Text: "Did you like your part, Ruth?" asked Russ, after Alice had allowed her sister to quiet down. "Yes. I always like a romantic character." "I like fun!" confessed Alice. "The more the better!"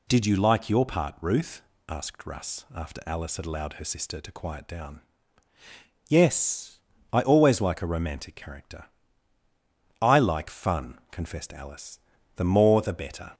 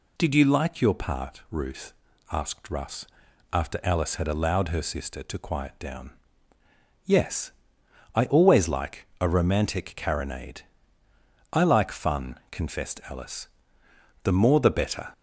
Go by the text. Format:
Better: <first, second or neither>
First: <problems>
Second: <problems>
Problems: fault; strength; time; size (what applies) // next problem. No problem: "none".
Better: first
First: none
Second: says "carronade" for "character"; at 9.9 s